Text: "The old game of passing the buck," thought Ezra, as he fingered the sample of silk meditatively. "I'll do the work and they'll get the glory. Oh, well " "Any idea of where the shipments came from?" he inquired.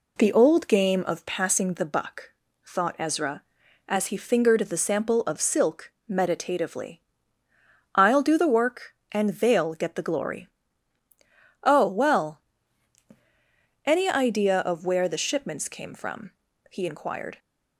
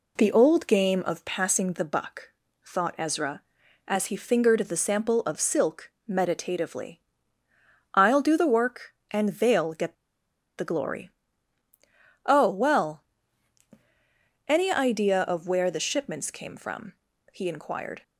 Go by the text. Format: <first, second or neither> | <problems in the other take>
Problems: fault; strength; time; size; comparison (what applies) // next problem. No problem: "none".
first | pauses between "silk" and "meditatively"; slight; at 5.9 s; 0.16 s long; slight in the first // pauses between "get" and "the"; noticeable; at 9.9 s; 0.63 s long